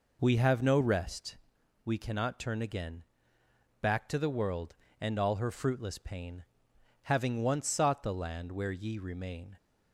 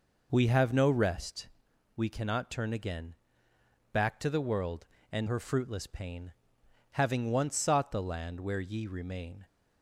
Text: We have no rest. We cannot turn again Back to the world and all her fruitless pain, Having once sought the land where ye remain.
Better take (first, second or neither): first